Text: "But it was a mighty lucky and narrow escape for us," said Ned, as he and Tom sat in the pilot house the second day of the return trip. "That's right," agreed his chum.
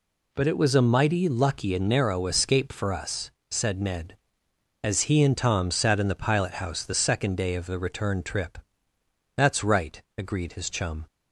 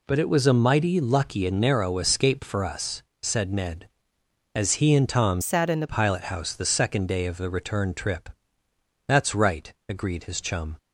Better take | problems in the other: first | changes voice from "sat" to "the"; from 5.4 to 5.8 s; 0.4 s long

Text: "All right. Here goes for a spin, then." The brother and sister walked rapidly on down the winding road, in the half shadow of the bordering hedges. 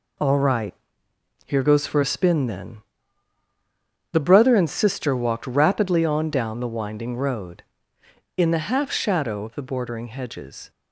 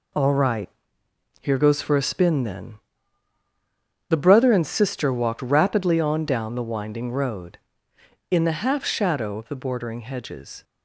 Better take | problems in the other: neither | none

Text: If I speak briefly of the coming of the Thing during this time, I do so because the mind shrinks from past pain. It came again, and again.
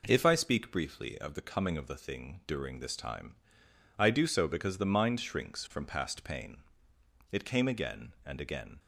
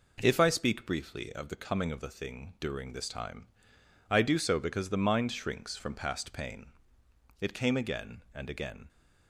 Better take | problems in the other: neither | none

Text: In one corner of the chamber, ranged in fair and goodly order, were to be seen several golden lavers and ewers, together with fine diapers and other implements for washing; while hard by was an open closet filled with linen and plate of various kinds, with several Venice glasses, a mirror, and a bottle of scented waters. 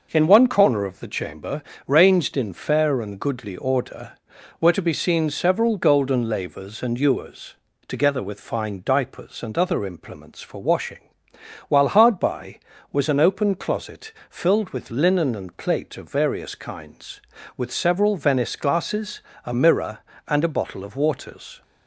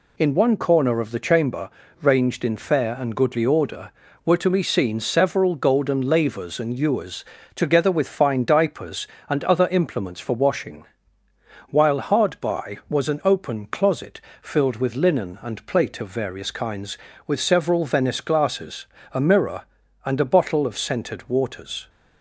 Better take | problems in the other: second | pauses between "closet" and "filled"; slight; at 14.1 s; 0.20 s long; slight in the second // skips "scented"; at 20.9 s

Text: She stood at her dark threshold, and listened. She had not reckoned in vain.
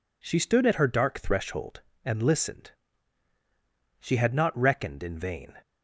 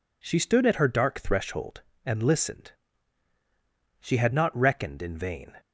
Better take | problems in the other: neither | none

